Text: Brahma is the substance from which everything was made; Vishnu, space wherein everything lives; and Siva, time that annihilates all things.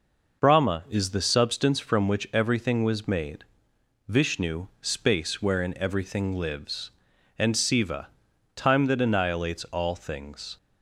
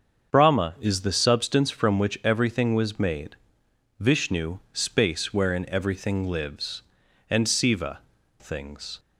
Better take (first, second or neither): first